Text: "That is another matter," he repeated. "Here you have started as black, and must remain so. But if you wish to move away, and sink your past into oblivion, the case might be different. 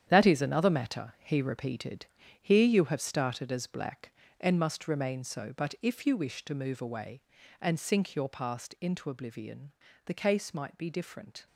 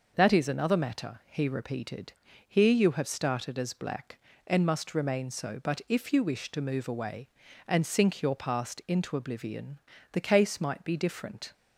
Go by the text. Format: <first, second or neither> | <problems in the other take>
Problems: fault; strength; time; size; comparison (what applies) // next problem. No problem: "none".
second | gets quieter; strong; throughout; 10 dB